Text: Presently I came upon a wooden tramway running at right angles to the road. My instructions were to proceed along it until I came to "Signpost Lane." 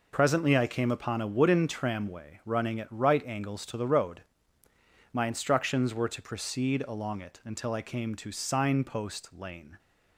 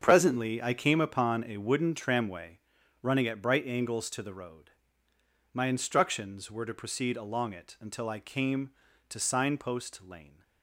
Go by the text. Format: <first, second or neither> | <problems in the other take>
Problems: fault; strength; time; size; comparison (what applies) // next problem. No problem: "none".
first | starts louder than the rest; until 1.0 s; 7 dB // pauses between "tramway" and "running"; at 2.5 s; 0.44 s long // says "bright" for "right"; at 3.4 s